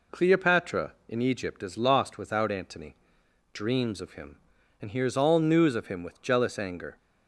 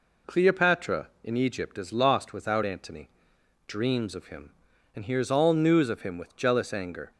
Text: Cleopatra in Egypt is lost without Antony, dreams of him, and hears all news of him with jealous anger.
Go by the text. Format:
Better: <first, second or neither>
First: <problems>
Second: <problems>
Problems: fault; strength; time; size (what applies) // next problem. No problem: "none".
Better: neither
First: none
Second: none